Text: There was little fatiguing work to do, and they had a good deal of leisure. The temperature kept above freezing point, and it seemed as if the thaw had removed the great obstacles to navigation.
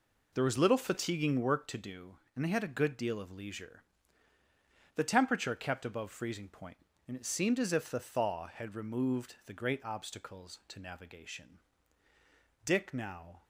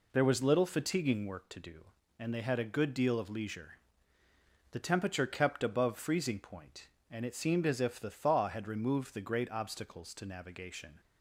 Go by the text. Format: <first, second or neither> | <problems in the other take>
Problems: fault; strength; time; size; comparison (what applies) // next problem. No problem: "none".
second | goes on to say "Dick now"; noticeable; from 12.6 s on; 0.78 s long